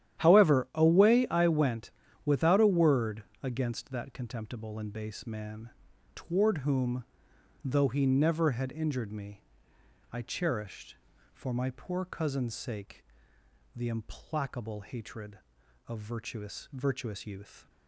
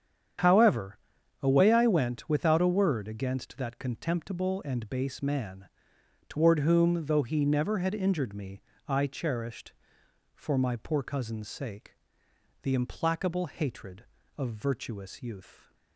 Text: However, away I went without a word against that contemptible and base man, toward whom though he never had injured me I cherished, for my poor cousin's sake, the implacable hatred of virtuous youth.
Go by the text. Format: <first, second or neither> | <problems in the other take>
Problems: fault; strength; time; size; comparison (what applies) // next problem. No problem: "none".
second | starts louder than the rest; strong; until 1.2 s; 11 dB; strong in the second // pauses between "went" and "without"; slight; at 1.9 s; 0.34 s long // pauses between "word" and "against"; slight; at 3.2 s; 0.18 s long // pauses between "whom" and "though"; noticeable; at 7.0 s; 0.58 s long // pauses between "me" and "I"; noticeable; at 9.4 s; 0.68 s long; slight in the second // says "virtuous" twice; at 16.7 s